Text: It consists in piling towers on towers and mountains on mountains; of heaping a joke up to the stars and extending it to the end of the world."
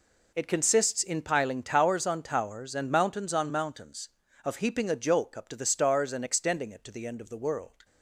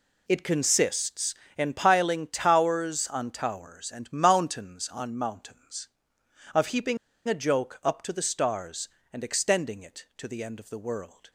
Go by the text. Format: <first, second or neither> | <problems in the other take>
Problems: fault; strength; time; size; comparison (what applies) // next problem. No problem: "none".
first | pauses between "heaping" and "a"; slight; at 6.9 s; 0.30 s long